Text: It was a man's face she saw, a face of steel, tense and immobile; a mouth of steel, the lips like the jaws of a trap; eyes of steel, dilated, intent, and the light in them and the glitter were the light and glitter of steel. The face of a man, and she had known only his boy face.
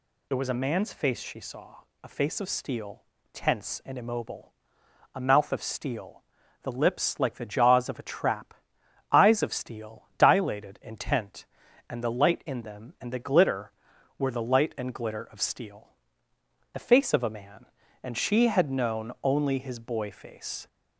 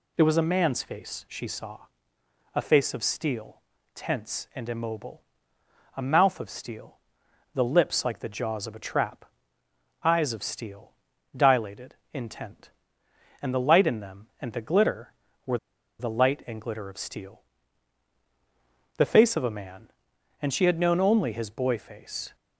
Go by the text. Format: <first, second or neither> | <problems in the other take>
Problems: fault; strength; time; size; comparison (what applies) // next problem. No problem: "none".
first | pauses between "were" and "the"; at 15.5 s; 0.42 s long